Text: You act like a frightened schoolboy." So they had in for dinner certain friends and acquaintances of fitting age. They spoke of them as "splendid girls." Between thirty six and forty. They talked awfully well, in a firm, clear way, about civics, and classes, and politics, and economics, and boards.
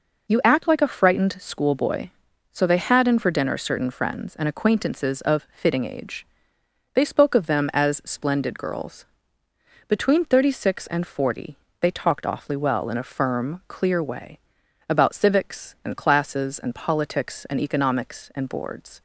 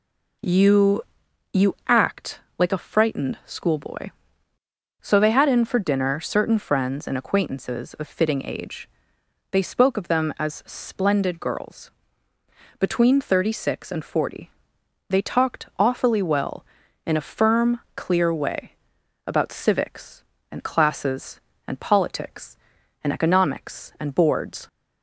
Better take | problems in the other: first | says "You" twice; at 1.5 s // pauses between "act" and "like"; slight; at 2.4 s; 0.16 s long

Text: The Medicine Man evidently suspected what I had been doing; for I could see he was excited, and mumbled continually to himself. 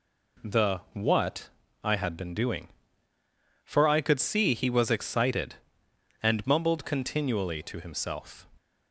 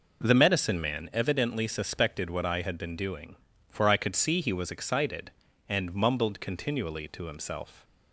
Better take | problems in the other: second | skips "Medicine Man evidently suspected"; at 0.8 s // pauses between "what" and "I"; slight; at 1.4 s; 0.32 s long

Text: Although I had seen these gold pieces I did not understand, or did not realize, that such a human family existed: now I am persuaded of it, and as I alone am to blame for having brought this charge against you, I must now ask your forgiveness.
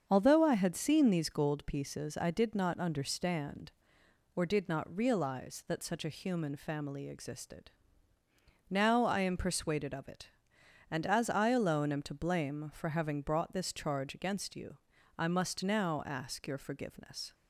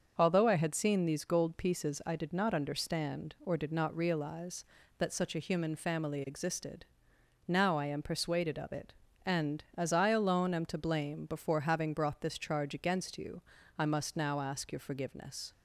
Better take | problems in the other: first | starts louder than the rest; until 1.1 s; 6.5 dB; also in the first // says "before" for "for"; at 11.2 s

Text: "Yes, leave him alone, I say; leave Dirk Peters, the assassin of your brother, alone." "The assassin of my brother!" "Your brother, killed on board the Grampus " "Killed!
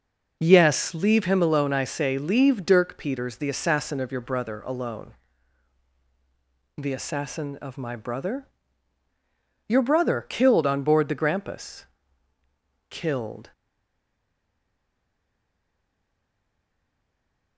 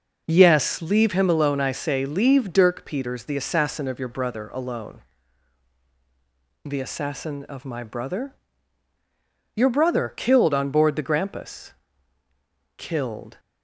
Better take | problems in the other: second | stays silent after the last word; strong; from 13.5 s on; 4.0 s long

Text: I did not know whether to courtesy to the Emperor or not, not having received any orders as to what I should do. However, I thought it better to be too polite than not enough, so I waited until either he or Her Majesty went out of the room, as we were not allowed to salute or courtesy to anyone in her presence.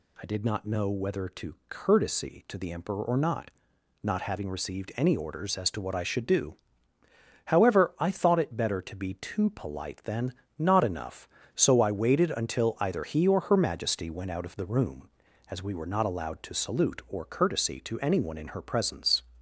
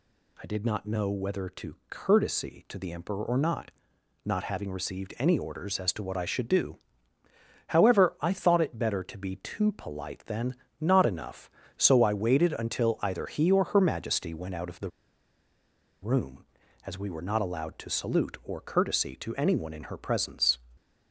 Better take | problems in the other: first | pauses between "than" and "not"; slight; at 10.5 s; 0.24 s long; slight in the first // pauses between "the" and "room"; at 14.9 s; 1.1 s long

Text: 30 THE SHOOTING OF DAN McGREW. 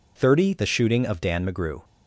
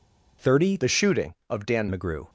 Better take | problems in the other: first | changes voice from "THE" to "DAN"; from 0.7 to 1.8 s; 1.1 s long

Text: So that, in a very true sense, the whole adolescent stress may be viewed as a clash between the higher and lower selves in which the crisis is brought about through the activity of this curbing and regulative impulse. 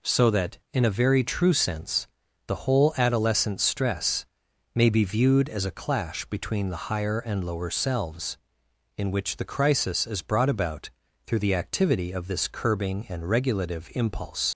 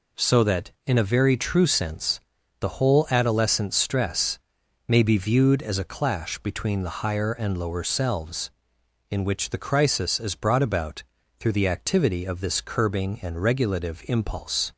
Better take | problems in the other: second | pauses between "stress" and "may"; noticeable; at 4.2 s; 0.50 s long; noticeable in the second // pauses between "about" and "through"; slight; at 10.8 s; 0.36 s long; slight in the second // leaves "impulse" unfinished; at 14.5 s; 55 ms

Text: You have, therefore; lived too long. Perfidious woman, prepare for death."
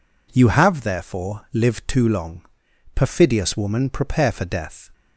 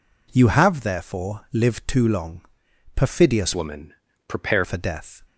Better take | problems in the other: first | changes voice from "woman" to "prepare"; from 3.5 to 4.6 s; 1.1 s long

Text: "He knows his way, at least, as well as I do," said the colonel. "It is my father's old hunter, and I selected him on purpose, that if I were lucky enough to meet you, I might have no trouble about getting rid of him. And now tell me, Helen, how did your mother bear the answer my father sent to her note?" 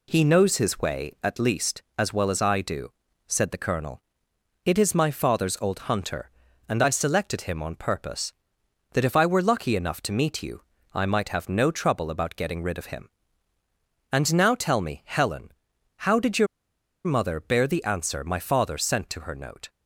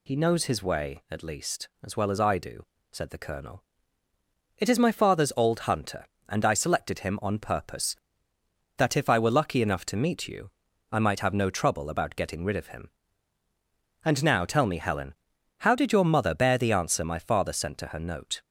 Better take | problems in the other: second | pauses between "your" and "mother"; noticeable; at 16.4 s; 0.60 s long

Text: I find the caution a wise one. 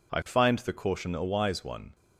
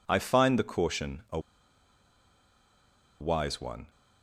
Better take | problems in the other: first | pauses between "a" and "wise"; strong; at 1.3 s; 1.8 s long

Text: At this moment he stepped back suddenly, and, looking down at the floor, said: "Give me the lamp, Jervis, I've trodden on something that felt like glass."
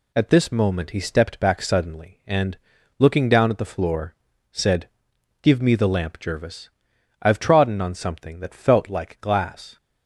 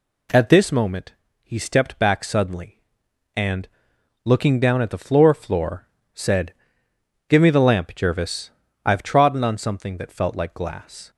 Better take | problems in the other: first | pauses between "moment" and "he"; slight; at 1.1 s; 0.28 s long // says "floor" twice; at 5.3 s

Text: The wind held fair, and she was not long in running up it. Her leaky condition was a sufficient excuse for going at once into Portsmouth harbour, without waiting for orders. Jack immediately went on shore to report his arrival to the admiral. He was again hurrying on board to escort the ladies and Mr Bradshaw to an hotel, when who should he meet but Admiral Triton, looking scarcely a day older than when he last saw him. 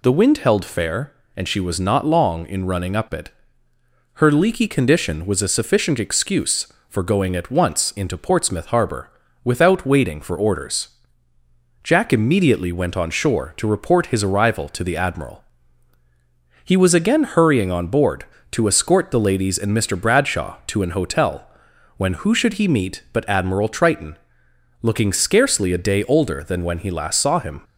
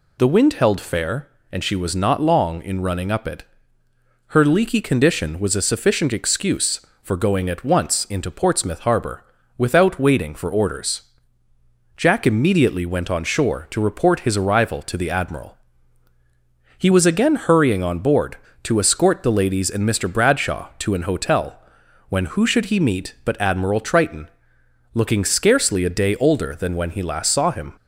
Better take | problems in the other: neither | none

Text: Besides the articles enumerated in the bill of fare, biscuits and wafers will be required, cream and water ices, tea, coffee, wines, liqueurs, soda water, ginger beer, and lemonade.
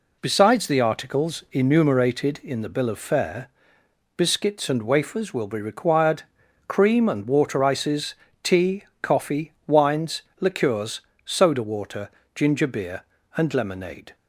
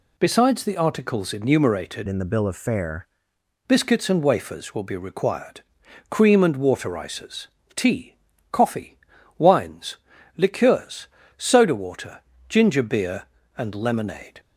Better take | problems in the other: first | changes voice from "in" to "fare"; from 2.0 to 3.0 s; 1.0 s long

